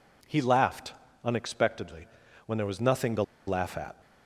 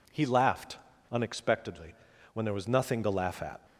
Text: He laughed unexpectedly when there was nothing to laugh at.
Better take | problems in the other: second | pauses between "laughed" and "unexpectedly"; slight; at 0.9 s; 0.30 s long; slight in the second // pauses between "unexpectedly" and "when"; at 2.0 s; 0.40 s long; also in the second // pauses between "to" and "laugh"; slight; at 3.2 s; 0.25 s long

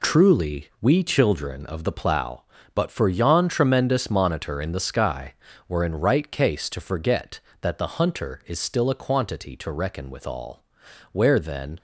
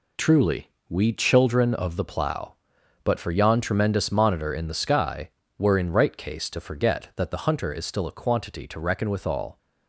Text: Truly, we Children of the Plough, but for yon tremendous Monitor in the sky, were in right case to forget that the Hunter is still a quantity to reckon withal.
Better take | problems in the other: second | goes on to say "Where then"; noticeable; from 11.1 s on; 0.66 s long

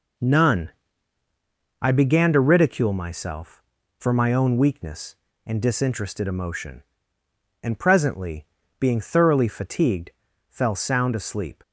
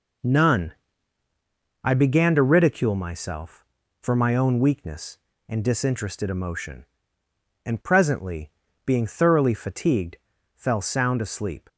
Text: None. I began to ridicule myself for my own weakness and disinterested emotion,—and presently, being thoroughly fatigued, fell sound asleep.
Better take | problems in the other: neither | none

